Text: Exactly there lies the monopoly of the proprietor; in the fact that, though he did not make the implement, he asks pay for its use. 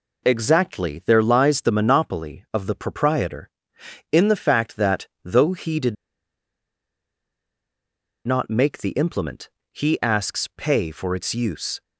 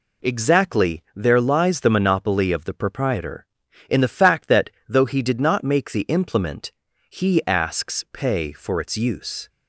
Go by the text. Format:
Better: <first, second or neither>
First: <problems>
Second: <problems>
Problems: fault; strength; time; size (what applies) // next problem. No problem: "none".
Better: second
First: pauses between "did" and "not"; strong; at 5.9 s; 2.3 s long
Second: none